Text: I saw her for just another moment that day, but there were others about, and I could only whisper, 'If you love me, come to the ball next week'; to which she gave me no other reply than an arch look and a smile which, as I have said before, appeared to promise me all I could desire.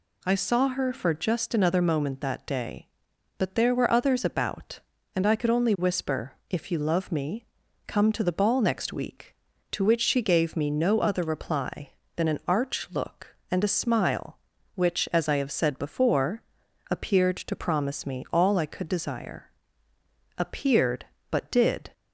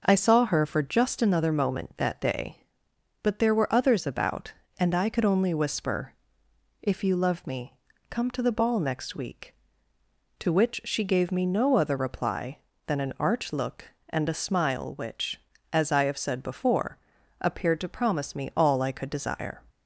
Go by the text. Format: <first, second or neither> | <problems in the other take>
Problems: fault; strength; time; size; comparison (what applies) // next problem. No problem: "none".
second | goes on to say "Appeared but did"; from 20.3 s on; 1.5 s long